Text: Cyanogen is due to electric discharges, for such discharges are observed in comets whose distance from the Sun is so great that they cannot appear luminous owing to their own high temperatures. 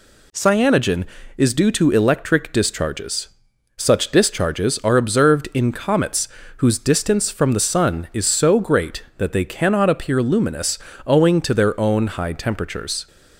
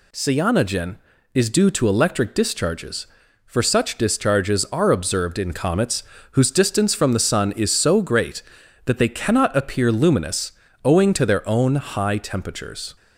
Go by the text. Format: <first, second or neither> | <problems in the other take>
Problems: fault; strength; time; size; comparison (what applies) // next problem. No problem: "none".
second | skips "for"; at 3.5 s // pauses between "comets" and "whose"; slight; at 6.2 s; 0.30 s long; slight in the second // pauses between "luminous" and "owing"; slight; at 10.7 s; 0.30 s long; slight in the second